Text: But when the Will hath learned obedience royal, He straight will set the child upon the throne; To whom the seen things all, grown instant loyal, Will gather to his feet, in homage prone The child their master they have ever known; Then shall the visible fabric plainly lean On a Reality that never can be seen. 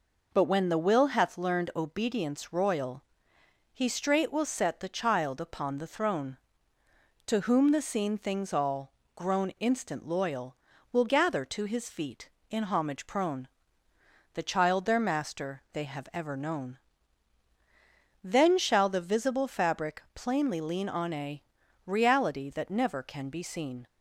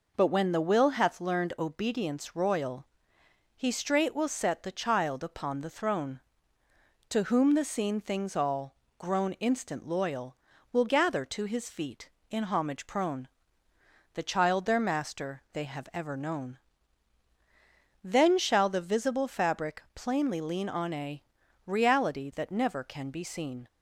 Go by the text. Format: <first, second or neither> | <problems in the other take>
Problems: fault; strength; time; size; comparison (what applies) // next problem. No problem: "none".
neither | pauses between "prone" and "The"; noticeable; the same in both // pauses between "a" and "Reality"; the same in both